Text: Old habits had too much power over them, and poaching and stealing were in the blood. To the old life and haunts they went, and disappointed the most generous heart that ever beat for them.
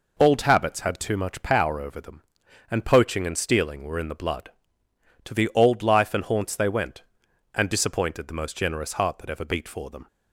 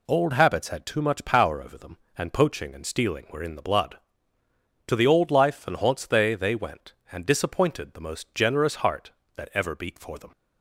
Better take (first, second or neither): first